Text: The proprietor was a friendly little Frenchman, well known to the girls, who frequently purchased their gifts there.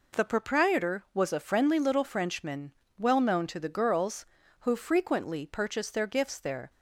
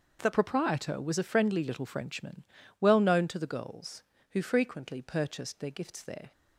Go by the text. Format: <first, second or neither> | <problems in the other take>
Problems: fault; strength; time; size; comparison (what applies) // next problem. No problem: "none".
first | starts louder than the rest; until 1.2 s; 6 dB // changes voice at "proprietor"; from 0.3 s on; 6.0 s long